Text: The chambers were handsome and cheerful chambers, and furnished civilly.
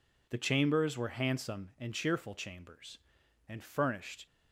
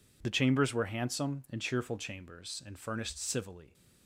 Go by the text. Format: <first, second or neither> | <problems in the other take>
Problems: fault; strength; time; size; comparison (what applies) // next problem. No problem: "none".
second | stops before "civilly"; at 4.2 s